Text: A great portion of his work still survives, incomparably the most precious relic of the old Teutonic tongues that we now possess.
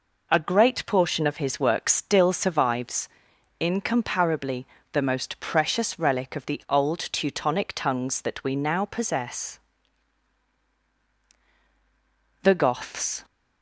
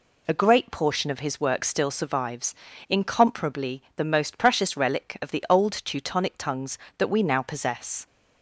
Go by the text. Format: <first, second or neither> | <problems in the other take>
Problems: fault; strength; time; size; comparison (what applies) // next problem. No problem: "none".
second | pauses between "incomparably" and "the"; slight; at 4.6 s; 0.26 s long // goes on to say "The Goths"; noticeable; from 12.4 s on; 0.82 s long